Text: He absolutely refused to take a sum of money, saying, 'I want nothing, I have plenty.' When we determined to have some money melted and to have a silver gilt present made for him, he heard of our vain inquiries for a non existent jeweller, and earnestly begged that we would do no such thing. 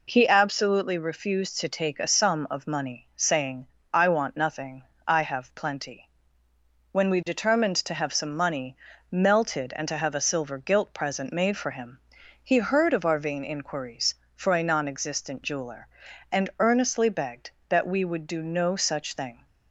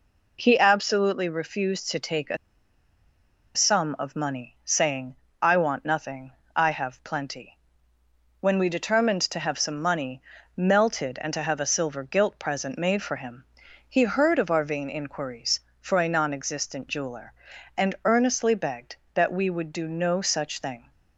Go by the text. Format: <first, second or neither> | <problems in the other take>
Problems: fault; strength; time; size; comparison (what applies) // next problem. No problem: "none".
first | pauses between "a" and "sum"; at 2.3 s; 1.1 s long // pauses between "money" and "melted"; slight; at 10.2 s; 0.34 s long; slight in the first